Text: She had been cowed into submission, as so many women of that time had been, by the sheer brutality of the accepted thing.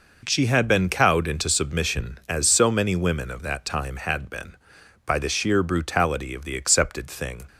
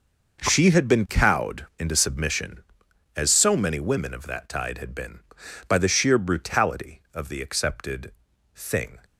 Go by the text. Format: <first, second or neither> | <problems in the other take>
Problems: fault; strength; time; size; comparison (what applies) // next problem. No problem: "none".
first | says "tide" for "time"; at 4.4 s // pauses between "accepted" and "thing"; at 8.1 s; 0.42 s long